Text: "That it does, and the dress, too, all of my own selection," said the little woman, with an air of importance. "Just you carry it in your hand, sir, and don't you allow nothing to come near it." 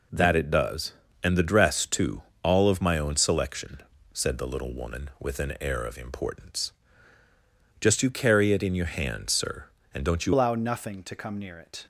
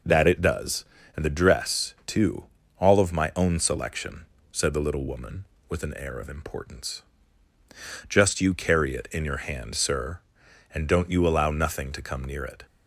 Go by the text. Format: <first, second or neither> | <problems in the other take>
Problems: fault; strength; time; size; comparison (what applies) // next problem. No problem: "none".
second | changes voice at "allow"; from 10.3 s on; 1.5 s long